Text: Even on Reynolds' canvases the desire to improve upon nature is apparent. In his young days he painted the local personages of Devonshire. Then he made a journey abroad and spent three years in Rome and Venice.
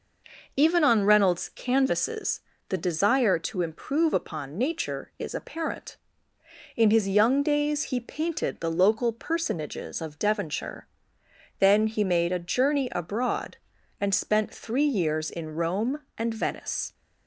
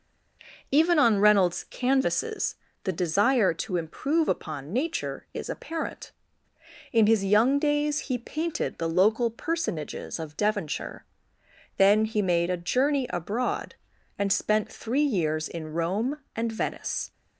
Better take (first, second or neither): neither